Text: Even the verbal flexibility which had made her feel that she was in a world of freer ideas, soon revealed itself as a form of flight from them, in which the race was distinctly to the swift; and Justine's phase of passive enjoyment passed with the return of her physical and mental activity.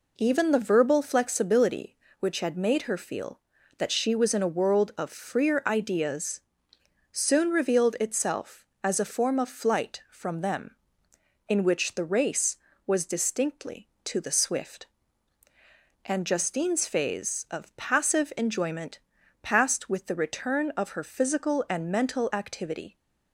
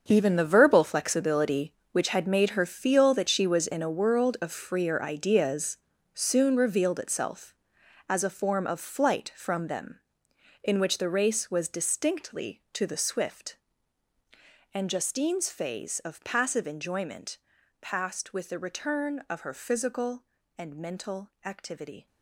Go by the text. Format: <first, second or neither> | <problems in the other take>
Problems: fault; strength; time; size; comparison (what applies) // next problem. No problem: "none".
first | gets quieter; strong; throughout; 12.5 dB // pauses between "enjoyment" and "passed"; at 17.3 s; 0.42 s long; also in the first